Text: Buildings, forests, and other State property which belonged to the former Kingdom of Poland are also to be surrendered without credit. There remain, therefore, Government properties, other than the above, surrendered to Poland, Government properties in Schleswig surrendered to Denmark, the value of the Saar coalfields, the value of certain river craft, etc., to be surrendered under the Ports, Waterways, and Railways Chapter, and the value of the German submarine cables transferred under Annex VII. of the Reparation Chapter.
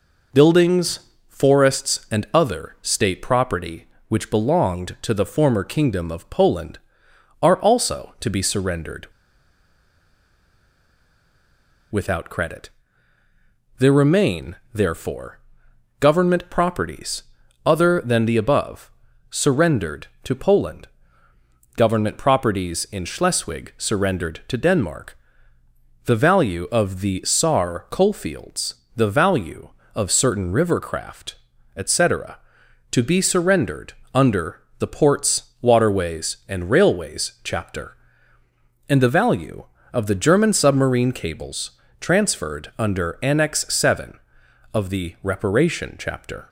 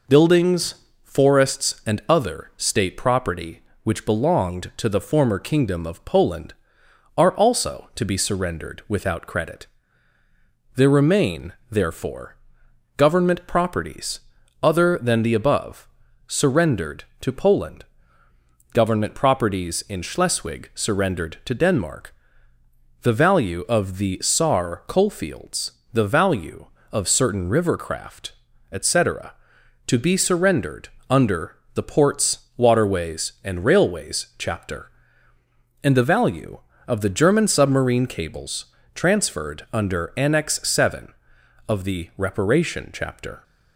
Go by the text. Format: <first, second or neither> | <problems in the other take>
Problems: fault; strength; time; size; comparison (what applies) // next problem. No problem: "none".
second | pauses between "surrendered" and "without"; strong; at 9.0 s; 2.8 s long // pauses between "surrendered" and "under"; slight; at 33.9 s; 0.22 s long; slight in the second // pauses between "under" and "the"; slight; at 34.6 s; 0.18 s long; slight in the second // pauses between "cables" and "transferred"; slight; at 41.7 s; 0.28 s long; slight in the second